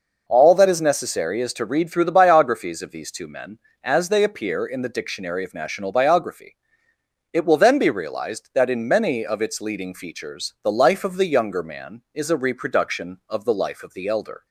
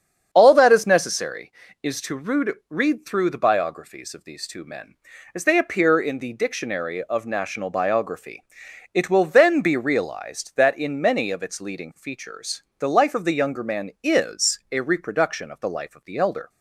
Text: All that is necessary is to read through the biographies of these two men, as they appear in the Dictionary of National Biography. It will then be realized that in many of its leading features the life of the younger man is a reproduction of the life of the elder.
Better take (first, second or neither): first